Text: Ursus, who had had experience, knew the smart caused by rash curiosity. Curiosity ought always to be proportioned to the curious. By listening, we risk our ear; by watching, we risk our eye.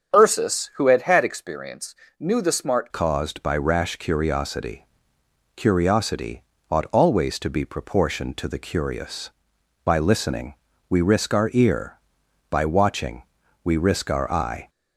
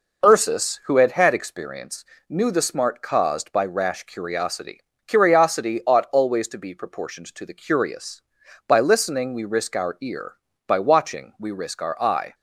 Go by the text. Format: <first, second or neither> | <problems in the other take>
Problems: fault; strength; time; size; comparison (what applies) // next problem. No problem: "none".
second | starts louder than the rest; strong; until 1.2 s; 7.5 dB // changes voice at "caused"; from 2.9 s on; 11.7 s long // pauses between "Curiosity" and "ought"; slight; at 6.4 s; 0.28 s long